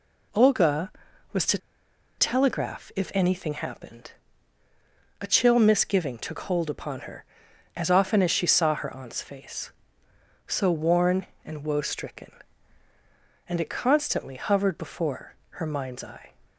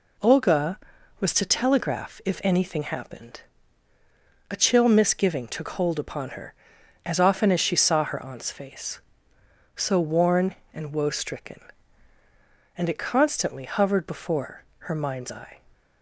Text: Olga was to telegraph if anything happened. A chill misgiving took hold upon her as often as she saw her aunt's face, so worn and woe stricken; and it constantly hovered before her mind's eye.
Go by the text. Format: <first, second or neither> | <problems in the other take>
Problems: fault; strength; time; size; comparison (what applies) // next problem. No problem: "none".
second | pauses between "to" and "telegraph"; noticeable; at 1.5 s; 0.60 s long // pauses between "before" and "her"; slight; at 15.3 s; 0.16 s long; slight in the second